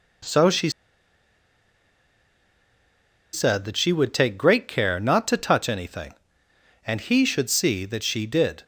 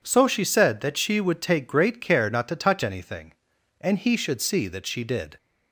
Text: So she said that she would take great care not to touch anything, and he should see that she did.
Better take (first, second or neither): second